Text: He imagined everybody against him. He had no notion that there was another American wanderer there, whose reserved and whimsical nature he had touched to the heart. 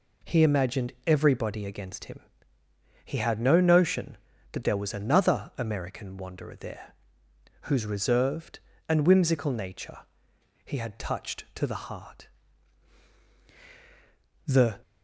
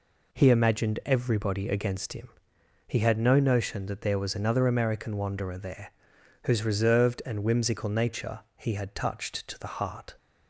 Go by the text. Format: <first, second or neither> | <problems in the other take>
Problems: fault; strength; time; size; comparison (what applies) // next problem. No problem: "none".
second | pauses between "nature" and "he"; noticeable; at 9.9 s; 0.66 s long; slight in the second // goes on to say "The"; slight; from 14.4 s on; 0.36 s long